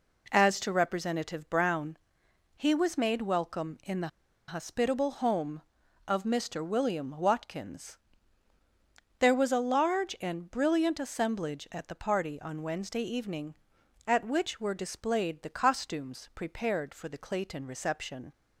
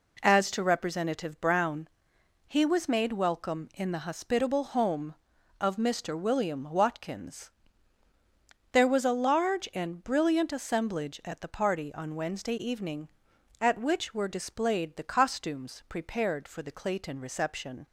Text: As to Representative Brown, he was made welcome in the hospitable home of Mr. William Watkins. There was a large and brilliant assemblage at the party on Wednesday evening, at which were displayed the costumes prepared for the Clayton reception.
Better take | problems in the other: second | pauses between "the" and "hospitable"; at 4.0 s; 0.39 s long

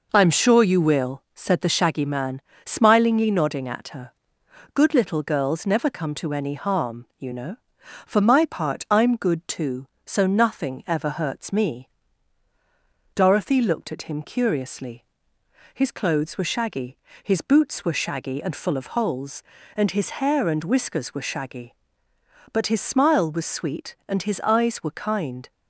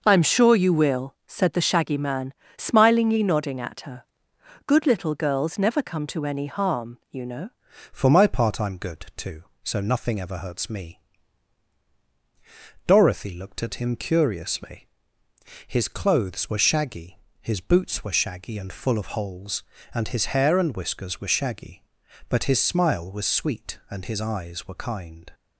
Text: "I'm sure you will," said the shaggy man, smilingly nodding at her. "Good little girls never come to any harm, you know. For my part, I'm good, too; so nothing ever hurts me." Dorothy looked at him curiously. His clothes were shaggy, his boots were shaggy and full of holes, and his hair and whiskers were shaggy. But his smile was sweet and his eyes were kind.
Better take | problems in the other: first | changes voice at "For"; from 7.9 s on; 17.4 s long

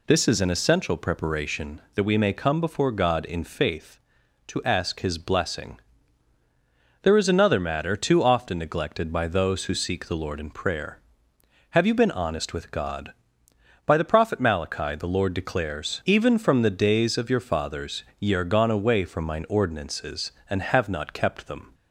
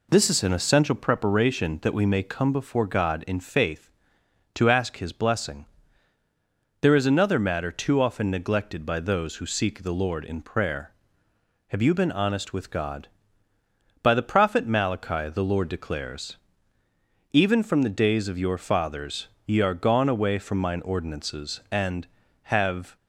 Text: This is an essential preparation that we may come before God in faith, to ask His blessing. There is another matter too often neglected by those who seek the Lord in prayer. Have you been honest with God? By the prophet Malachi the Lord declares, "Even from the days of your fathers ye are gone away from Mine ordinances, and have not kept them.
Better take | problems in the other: first | pauses between "fathers" and "ye"; slight; at 19.2 s; 0.18 s long; slight in the first // stops before "not kept them"; at 22.9 s

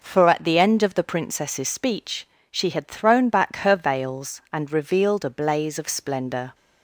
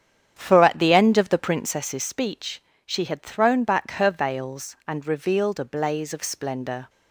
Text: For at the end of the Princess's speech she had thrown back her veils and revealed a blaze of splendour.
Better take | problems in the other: first | starts louder than the rest; strong; until 2.0 s; 8.5 dB // pauses between "speech" and "she"; slight; at 2.6 s; 0.24 s long; slight in the first

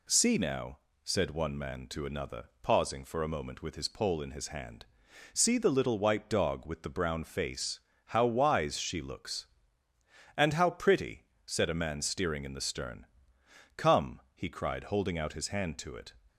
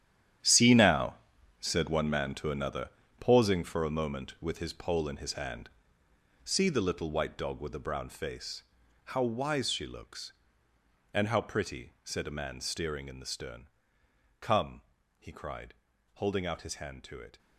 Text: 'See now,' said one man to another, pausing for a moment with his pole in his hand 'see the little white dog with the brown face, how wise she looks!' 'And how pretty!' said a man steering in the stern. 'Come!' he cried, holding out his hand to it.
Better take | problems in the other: first | gets quieter; strong; throughout; 12.5 dB // pauses between "hand" and "see"; noticeable; at 5.6 s; 0.76 s long; noticeable in the first

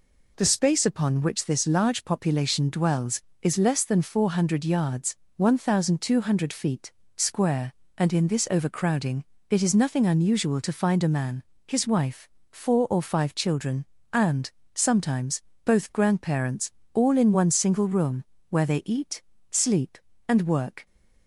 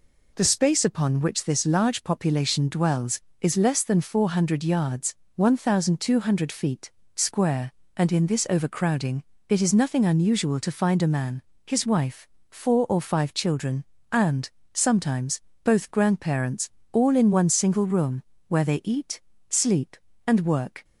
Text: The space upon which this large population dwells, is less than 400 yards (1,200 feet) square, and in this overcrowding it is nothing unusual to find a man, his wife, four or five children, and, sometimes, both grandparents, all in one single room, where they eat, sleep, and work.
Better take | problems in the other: neither | pauses between "overcrowding" and "it"; slight; the same in both

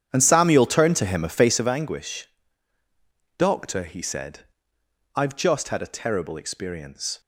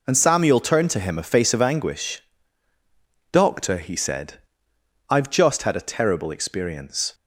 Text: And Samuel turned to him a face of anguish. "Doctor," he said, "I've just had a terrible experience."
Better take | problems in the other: second | starts louder than the rest; strong; until 1.6 s; 9.5 dB

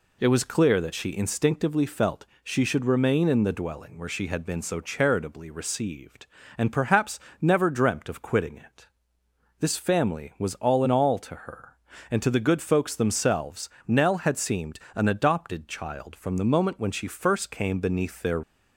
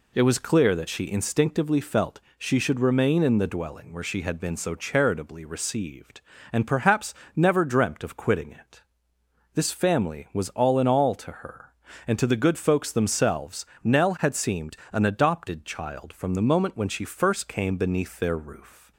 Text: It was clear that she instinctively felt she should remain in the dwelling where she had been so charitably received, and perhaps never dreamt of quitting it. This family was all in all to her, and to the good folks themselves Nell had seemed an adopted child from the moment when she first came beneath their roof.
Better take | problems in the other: second | pauses between "felt" and "she"; slight; at 2.2 s; 0.18 s long; slight in the second // pauses between "perhaps" and "never"; slight; at 7.1 s; 0.22 s long; slight in the second // pauses between "themselves" and "Nell"; slight; at 13.6 s; 0.18 s long; slight in the second // pauses between "seemed" and "an"; slight; at 14.7 s; 0.16 s long; slight in the second // stops before "roof"; at 18.4 s

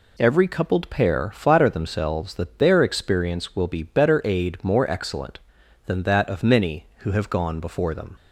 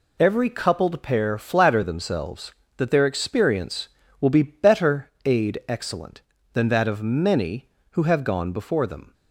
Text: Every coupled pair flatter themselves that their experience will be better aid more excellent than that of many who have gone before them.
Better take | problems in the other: first | skips "more"; at 5.6 s

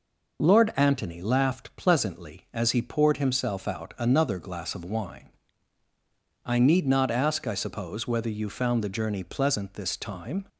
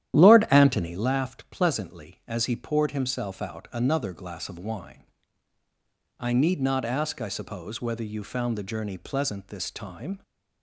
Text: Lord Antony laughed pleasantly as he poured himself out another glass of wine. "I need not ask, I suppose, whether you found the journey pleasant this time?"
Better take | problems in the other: first | starts louder than the rest; strong; until 1.1 s; 11.5 dB

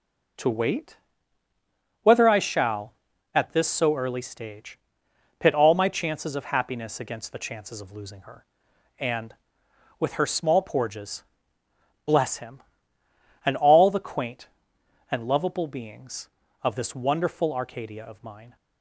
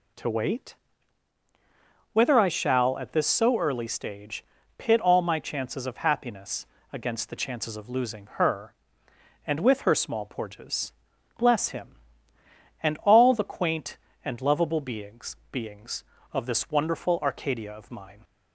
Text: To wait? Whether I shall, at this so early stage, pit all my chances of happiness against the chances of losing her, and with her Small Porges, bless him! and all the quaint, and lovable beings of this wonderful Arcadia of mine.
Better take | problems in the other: first | pauses between "happiness" and "against"; slight; at 6.6 s; 0.26 s long // says "beings" twice; at 15.4 s

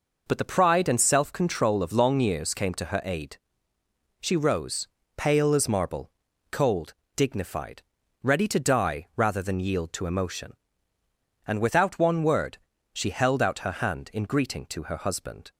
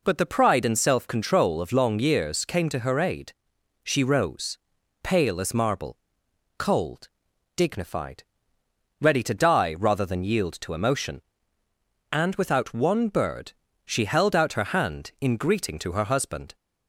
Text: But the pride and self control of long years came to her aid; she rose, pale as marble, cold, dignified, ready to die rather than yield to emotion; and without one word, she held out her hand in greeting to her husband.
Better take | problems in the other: first | says "bird" for "word"; at 13.0 s

